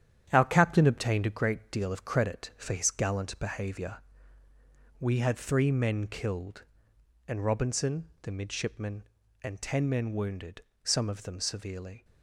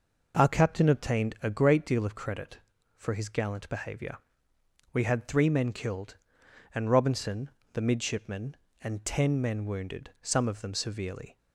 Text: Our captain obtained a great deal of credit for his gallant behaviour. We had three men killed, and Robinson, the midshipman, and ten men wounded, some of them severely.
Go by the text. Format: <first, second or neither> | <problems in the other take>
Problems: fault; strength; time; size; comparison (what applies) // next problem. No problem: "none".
second | gets quieter; throughout; 6.5 dB